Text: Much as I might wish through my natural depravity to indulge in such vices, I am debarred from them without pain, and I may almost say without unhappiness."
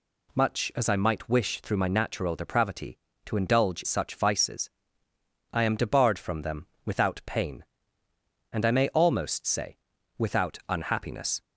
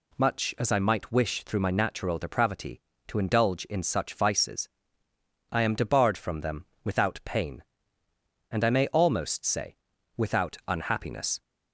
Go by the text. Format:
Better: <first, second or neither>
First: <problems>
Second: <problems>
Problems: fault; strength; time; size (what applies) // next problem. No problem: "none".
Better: second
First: skips "in"; at 3.8 s // pauses between "them" and "without"; slight; at 6.6 s; 0.18 s long // pauses between "say" and "without"; at 9.7 s; 0.42 s long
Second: pauses between "them" and "without"; slight; at 6.6 s; 0.18 s long // pauses between "say" and "without"; at 9.7 s; 0.42 s long